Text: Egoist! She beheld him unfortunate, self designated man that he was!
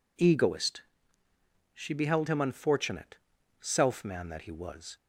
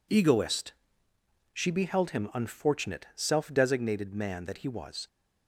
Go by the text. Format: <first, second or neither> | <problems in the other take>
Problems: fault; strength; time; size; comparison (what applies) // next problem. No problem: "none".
second | skips "designated"; at 4.0 s